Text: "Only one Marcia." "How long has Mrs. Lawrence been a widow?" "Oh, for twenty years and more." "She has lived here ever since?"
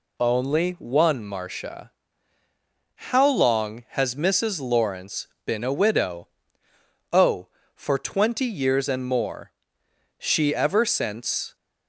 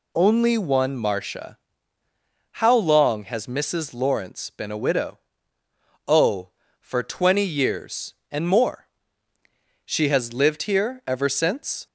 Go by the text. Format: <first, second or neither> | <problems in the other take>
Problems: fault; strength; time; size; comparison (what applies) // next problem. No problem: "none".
second | pauses between "Lawrence" and "been"; slight; at 5.2 s; 0.18 s long // skips "has lived here"; at 10.5 s